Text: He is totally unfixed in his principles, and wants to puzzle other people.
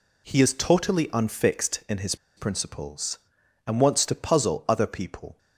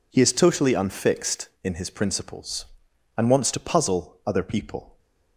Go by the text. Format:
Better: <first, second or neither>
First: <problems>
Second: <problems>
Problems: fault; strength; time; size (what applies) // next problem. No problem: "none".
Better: second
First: pauses between "his" and "principles"; slight; at 2.1 s; 0.21 s long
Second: none